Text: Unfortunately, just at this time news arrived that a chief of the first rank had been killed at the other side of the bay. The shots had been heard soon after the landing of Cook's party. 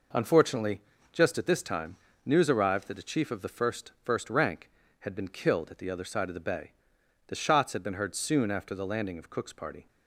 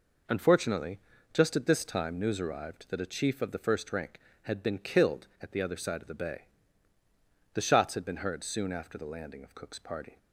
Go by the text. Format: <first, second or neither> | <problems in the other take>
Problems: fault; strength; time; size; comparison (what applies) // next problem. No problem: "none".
second | pauses between "time" and "news"; slight; at 1.9 s; 0.30 s long // says "first" twice; at 4.0 s